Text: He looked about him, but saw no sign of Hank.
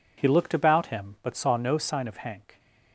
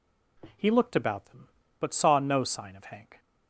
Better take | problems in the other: first | says "them" for "him"; at 1.2 s

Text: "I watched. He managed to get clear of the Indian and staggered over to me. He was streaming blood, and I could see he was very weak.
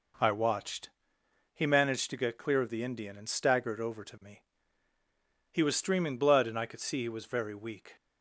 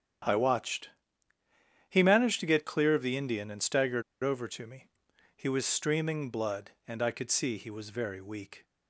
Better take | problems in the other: first | starts louder than the rest; strong; until 2.2 s; 9.5 dB // pauses between "staggered" and "over"; slight; at 4.0 s; 0.21 s long

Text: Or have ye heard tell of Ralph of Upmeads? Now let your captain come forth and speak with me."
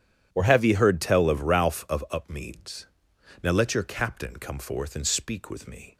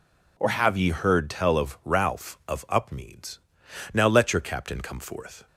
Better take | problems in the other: first | stops before "and speak with me"; at 5.4 s

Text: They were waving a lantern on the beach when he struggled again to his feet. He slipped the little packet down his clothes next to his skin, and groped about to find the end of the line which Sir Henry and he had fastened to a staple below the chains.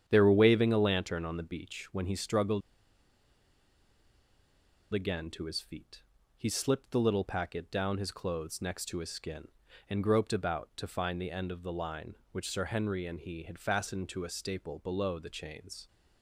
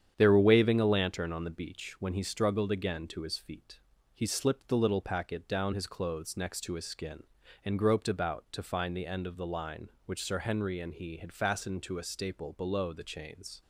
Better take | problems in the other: second | starts louder than the rest; strong; until 1.0 s; 8.5 dB; strong in the second // pauses between "struggled" and "again"; strong; at 2.6 s; 2.3 s long

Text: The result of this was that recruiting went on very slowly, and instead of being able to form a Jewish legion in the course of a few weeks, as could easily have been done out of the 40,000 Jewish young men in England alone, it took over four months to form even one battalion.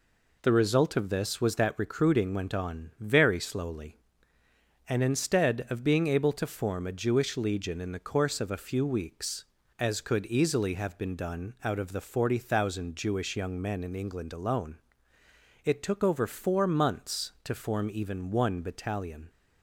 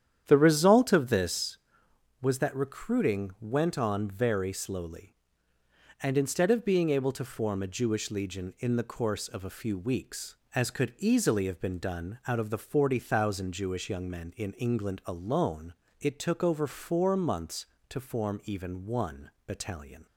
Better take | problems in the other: first | starts louder than the rest; strong; until 1.5 s; 9.5 dB // pauses between "one" and "battalion"; slight; at 19.2 s; 0.16 s long

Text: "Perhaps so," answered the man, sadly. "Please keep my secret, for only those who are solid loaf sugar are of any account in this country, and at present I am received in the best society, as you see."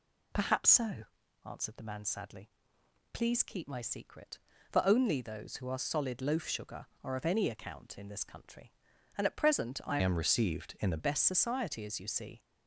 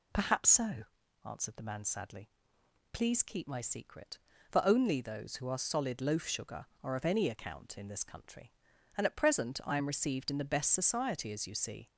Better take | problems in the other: second | changes voice from "am" to "the"; from 9.9 to 10.9 s; 1.0 s long

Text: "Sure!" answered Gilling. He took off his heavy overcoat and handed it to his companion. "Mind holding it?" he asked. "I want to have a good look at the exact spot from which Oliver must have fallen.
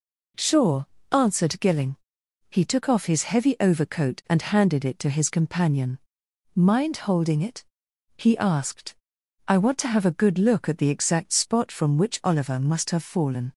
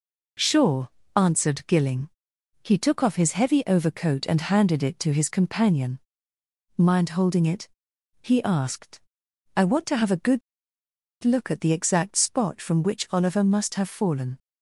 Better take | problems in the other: first | pauses between "good" and "look"; noticeable; at 10.4 s; 0.83 s long

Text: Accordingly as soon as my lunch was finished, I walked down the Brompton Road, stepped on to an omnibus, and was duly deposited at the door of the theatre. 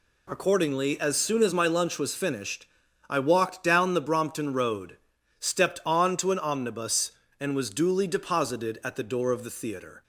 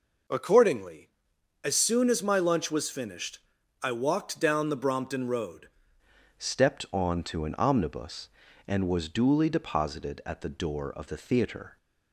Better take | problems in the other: first | changes voice at "stepped"; from 6.3 s on; 5.4 s long

